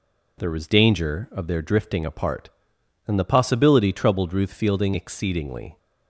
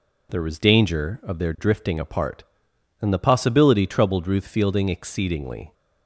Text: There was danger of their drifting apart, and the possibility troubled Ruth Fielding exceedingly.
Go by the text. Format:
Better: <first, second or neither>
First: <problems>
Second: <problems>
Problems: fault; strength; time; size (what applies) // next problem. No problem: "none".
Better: neither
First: none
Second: none